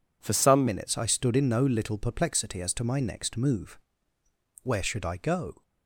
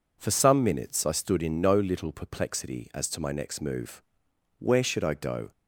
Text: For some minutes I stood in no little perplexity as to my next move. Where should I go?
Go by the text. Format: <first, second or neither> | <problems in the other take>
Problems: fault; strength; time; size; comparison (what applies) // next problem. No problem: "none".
second | changes voice at "minutes"; from 0.6 s on; 5.0 s long